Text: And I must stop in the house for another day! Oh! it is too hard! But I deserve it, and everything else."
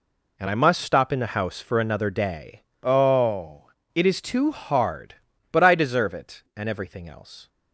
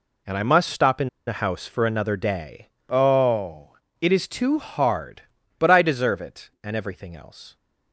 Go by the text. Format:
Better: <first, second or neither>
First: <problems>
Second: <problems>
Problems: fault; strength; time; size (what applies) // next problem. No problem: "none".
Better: first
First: none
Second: pauses between "in" and "the"; slight; at 1.0 s; 0.19 s long